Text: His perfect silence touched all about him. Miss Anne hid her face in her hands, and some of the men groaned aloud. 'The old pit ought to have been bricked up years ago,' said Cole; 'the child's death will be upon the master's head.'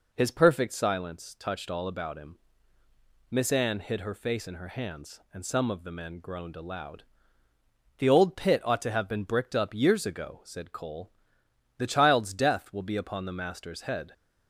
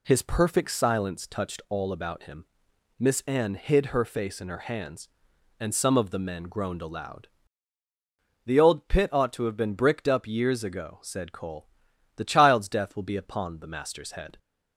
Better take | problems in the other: neither | none

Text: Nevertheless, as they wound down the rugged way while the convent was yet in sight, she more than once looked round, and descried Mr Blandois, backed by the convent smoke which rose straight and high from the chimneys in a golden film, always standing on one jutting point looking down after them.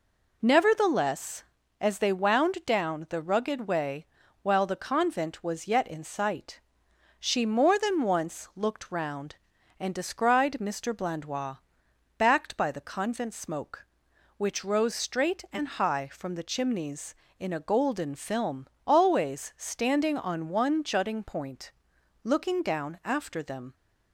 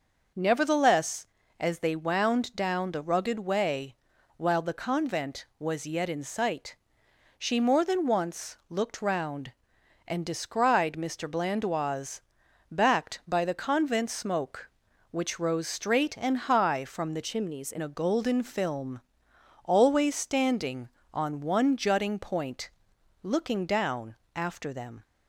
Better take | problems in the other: first | pauses between "way" and "while"; at 3.9 s; 0.42 s long; also in the first // changes voice from "chimneys" to "in"; from 17.2 to 17.7 s; 0.5 s long // pauses between "point" and "looking"; noticeable; at 22.7 s; 0.50 s long; noticeable in the first // pauses between "down" and "after"; slight; at 24.1 s; 0.18 s long

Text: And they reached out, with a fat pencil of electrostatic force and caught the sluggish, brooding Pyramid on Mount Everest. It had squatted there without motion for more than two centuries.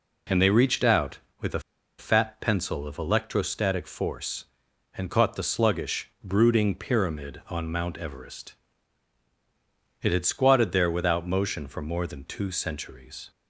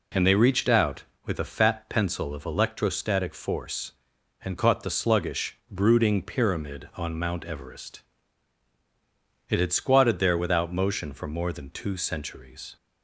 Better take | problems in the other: second | pauses between "a" and "fat"; at 1.5 s; 0.38 s long

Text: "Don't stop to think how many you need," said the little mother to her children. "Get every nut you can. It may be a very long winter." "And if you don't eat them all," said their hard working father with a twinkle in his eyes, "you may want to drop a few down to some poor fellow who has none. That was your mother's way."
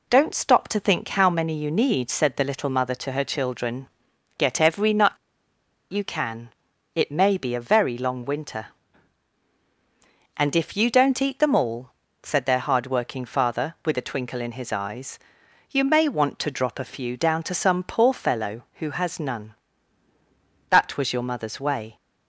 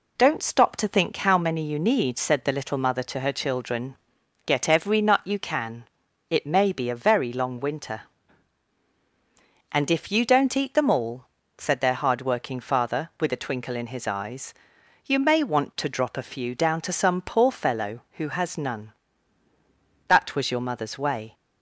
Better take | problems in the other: second | pauses between "nut" and "you"; noticeable; at 5.1 s; 0.78 s long

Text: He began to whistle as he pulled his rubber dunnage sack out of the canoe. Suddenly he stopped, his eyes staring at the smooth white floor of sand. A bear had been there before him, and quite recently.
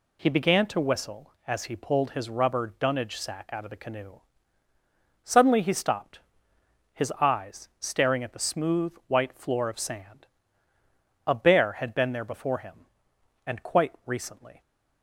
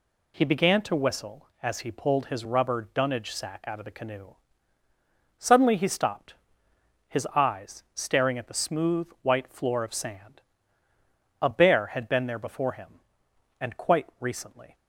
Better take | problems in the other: neither | pauses between "smooth" and "white"; slight; the same in both

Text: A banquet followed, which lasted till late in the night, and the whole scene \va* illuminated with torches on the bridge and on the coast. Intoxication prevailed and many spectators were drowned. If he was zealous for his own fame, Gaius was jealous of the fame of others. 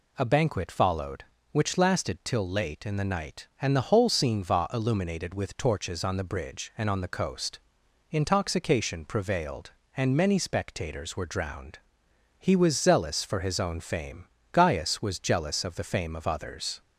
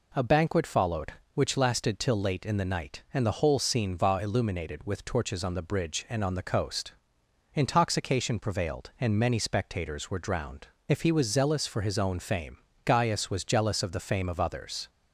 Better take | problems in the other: second | skips "If"; at 12.0 s

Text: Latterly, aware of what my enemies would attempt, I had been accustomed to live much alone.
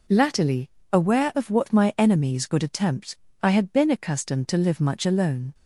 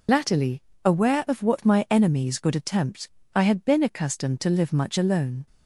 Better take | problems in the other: first | loses the start of "Latterly"; at 0.0 s; 75 ms

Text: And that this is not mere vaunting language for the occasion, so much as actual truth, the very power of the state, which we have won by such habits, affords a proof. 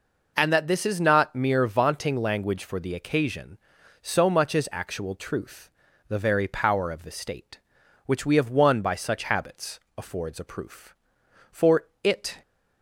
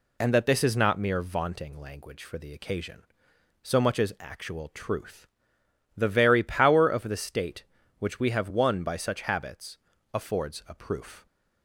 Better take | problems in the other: second | goes on to say "For it"; noticeable; from 11.5 s on; 0.90 s long

